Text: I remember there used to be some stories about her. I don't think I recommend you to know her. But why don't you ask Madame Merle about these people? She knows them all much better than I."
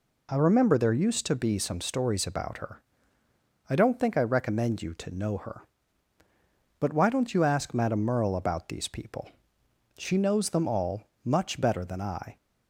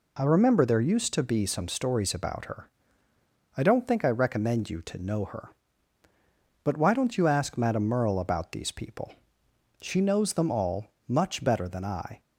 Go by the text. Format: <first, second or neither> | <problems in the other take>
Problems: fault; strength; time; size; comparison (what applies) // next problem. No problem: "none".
neither | pauses between "all" and "much"; slight; the same in both